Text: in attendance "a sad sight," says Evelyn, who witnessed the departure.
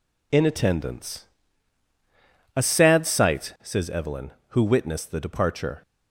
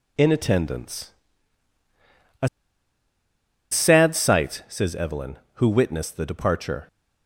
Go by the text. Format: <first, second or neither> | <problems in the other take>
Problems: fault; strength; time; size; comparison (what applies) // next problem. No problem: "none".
first | pauses between "attendance" and "a"; strong; at 1.1 s; 1.3 s long; strong in the first // pauses between "a" and "sad"; at 2.4 s; 1.2 s long